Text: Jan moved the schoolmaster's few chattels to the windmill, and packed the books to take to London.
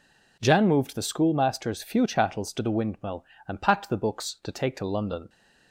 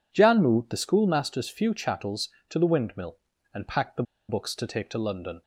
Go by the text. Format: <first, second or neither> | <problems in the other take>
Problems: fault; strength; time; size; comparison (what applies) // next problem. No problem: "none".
first | pauses between "the" and "books"; slight; at 4.0 s; 0.26 s long